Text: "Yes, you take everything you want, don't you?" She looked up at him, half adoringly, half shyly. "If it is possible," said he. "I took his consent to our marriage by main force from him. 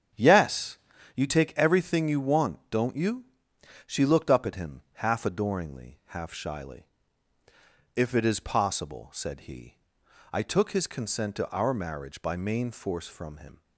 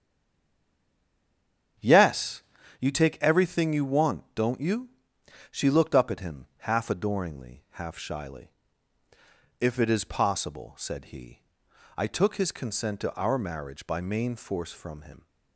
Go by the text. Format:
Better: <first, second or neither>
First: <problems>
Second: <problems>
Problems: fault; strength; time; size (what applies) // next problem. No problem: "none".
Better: first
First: starts louder than the rest; strong; until 1.5 s; 8 dB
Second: stays silent before the first word; noticeable; until 1.7 s; 1.7 s long // starts louder than the rest; strong; until 3.1 s; 8 dB